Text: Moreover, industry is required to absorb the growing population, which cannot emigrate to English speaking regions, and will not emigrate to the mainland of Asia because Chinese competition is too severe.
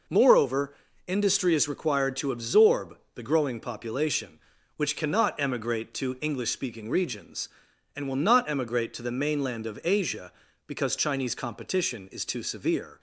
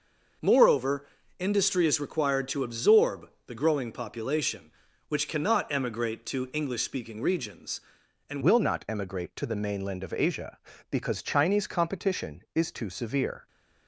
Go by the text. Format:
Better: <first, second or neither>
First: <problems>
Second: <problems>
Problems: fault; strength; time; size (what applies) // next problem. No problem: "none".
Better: first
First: pauses between "absorb" and "the"; slight; at 2.9 s; 0.18 s long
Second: pauses between "absorb" and "the"; slight; at 3.2 s; 0.18 s long // changes voice at "will"; from 8.4 s on; 5.0 s long